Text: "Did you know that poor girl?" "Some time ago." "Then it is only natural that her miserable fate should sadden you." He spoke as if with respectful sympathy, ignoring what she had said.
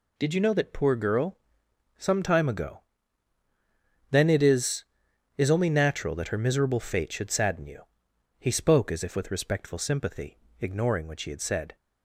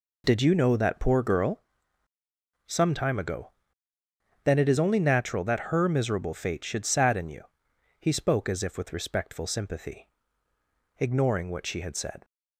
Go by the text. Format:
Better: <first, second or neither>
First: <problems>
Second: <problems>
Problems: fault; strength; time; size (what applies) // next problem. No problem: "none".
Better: second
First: says "is" twice; at 5.3 s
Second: none